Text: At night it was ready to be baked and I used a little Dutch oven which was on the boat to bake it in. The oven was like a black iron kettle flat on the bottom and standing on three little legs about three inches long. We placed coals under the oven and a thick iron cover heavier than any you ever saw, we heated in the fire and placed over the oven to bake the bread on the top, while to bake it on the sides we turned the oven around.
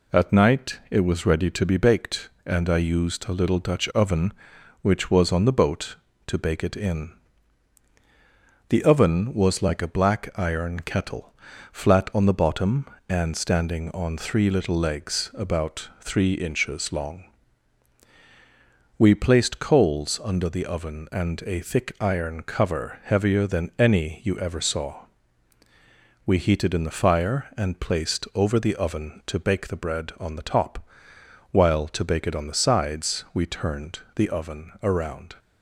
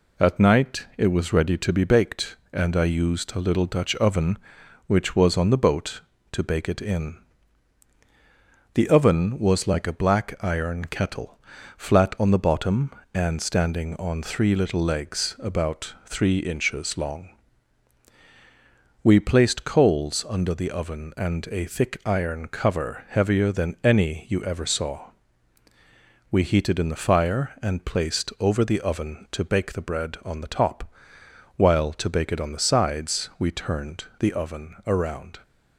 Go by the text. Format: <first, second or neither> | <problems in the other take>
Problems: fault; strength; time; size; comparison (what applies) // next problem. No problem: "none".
neither | pauses between "kettle" and "flat"; the same in both // pauses between "turned" and "the"; slight; the same in both